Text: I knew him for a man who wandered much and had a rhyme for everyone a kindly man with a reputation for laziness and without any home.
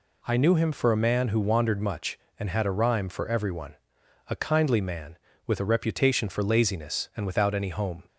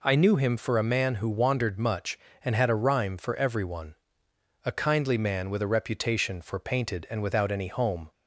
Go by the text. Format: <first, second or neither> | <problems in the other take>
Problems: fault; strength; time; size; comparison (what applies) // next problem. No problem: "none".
first | pauses between "everyone" and "a"; noticeable; at 3.9 s; 0.70 s long; noticeable in the first // says "painted" for "laziness"; at 6.5 s